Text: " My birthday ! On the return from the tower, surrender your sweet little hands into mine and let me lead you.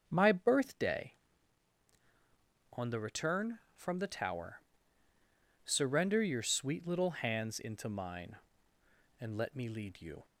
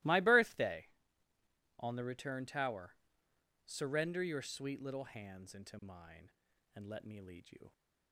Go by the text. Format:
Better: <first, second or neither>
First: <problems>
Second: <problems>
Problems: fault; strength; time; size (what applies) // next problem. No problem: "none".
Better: first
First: starts louder than the rest; until 1.1 s; 7 dB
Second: starts louder than the rest; strong; until 1.9 s; 20 dB // skips "from the"; at 2.4 s